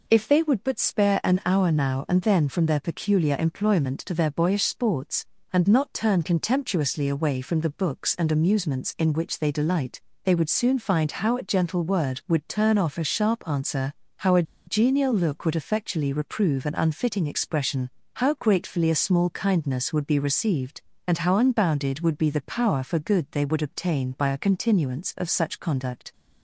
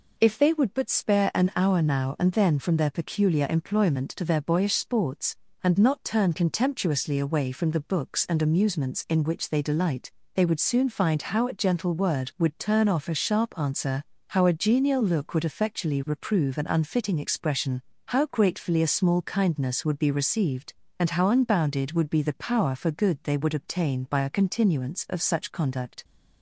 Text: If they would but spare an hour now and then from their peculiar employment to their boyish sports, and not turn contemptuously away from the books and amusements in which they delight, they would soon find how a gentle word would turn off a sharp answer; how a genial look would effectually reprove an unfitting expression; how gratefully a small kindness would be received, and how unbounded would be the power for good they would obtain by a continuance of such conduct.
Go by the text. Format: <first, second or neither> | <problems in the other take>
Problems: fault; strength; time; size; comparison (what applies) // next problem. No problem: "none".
second | pauses between "a" and "genial"; slight; at 14.4 s; 0.24 s long